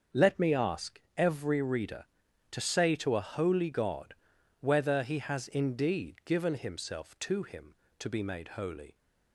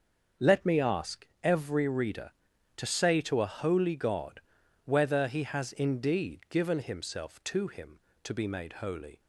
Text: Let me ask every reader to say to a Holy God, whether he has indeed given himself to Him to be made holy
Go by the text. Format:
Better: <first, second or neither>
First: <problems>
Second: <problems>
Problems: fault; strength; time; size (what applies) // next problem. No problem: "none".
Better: neither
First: starts louder than the rest; until 1.3 s; 6.5 dB // pauses between "ask" and "every"; slight; at 0.9 s; 0.16 s long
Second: starts louder than the rest; until 1.5 s; 6.5 dB // pauses between "ask" and "every"; slight; at 1.2 s; 0.16 s long